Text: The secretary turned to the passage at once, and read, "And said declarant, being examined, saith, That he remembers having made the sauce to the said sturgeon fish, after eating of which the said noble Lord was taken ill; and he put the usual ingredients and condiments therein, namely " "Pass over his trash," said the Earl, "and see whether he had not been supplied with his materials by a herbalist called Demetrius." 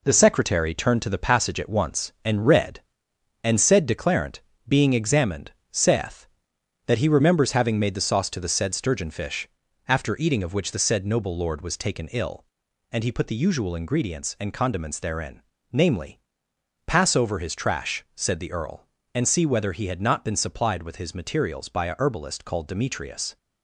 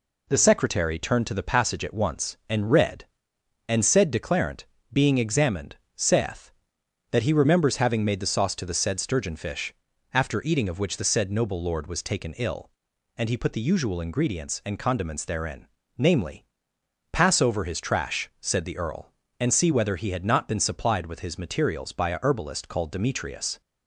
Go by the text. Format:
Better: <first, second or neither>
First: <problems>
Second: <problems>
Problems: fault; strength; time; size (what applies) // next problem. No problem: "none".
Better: second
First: gets quieter; strong; throughout; 8 dB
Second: none